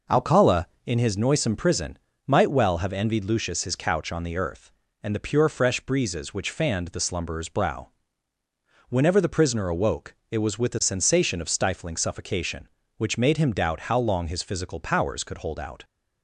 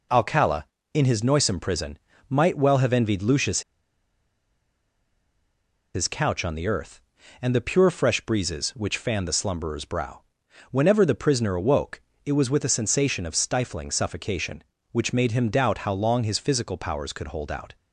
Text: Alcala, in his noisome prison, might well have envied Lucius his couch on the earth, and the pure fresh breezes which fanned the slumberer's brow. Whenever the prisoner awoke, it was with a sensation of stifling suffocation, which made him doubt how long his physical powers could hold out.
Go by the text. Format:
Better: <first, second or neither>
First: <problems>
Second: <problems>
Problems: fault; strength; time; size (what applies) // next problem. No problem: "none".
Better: first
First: none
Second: pauses between "Lucius" and "his"; strong; at 3.6 s; 2.3 s long